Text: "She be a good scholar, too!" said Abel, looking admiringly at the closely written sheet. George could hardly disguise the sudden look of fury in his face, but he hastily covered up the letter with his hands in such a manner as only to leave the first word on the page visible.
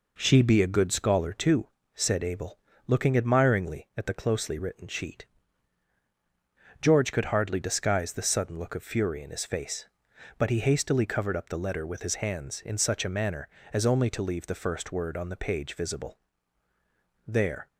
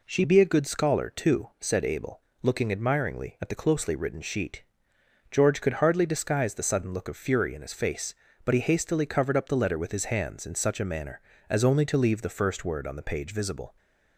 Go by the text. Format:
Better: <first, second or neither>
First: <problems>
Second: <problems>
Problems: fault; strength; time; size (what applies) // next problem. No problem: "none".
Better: second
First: goes on to say "There"; slight; from 17.2 s on; 0.40 s long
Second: none